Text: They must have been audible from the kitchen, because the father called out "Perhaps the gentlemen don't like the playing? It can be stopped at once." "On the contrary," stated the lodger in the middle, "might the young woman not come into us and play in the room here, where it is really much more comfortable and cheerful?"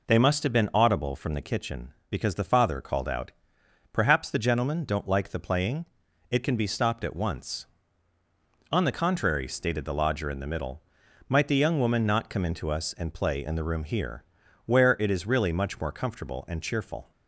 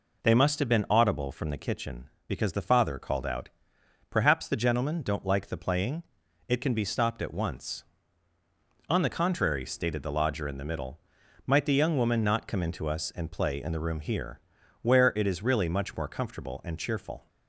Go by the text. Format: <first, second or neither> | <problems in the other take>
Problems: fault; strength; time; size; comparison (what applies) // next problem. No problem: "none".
neither | pauses between "out" and "Perhaps"; noticeable; the same in both